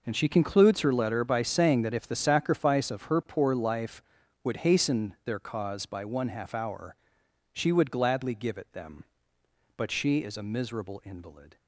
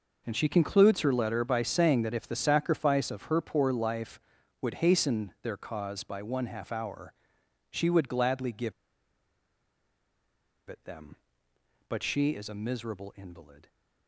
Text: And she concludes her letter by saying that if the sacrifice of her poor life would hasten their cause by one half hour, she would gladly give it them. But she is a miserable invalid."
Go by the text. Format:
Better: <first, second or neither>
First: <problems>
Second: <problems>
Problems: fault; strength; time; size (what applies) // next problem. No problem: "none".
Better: first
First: none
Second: pauses between "give" and "it"; strong; at 8.7 s; 1.9 s long